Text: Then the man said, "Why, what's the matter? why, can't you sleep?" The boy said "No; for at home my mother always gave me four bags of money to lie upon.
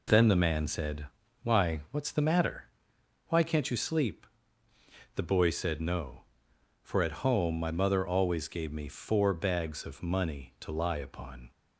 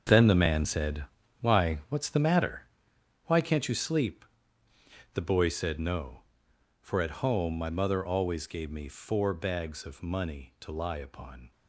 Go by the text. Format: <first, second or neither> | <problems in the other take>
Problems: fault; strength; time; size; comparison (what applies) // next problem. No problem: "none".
first | gets quieter; strong; throughout; 12 dB